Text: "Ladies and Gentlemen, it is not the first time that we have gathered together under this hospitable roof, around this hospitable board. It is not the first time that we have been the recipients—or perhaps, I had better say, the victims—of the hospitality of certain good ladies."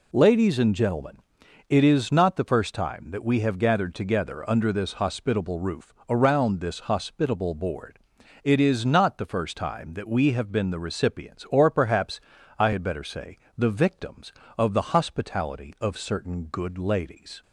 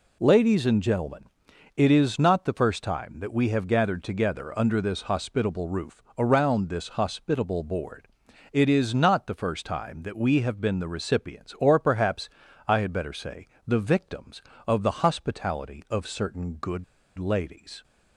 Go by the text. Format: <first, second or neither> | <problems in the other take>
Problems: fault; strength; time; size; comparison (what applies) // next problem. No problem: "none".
first | pauses between "good" and "ladies"; slight; at 16.8 s; 0.34 s long